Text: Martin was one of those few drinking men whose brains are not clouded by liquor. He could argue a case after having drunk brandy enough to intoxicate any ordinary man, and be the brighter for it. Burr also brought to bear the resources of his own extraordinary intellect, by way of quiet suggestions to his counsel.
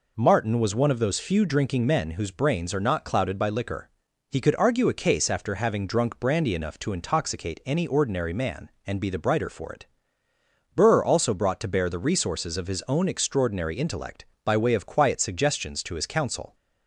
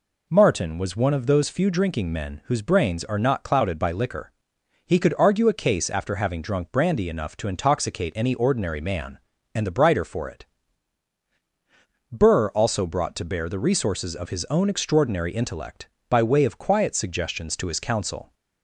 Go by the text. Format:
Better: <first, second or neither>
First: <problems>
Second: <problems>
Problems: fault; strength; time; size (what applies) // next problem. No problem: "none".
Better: first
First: none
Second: skips "be"; at 9.6 s